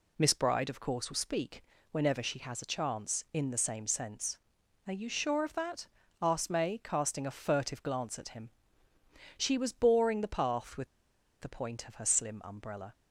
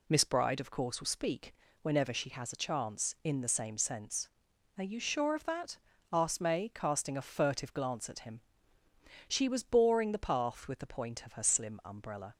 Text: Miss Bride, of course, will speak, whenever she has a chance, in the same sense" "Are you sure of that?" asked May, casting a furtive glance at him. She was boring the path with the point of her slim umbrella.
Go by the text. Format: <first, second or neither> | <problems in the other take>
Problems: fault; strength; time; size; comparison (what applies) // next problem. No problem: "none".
second | pauses between "with" and "the"; noticeable; at 10.8 s; 0.53 s long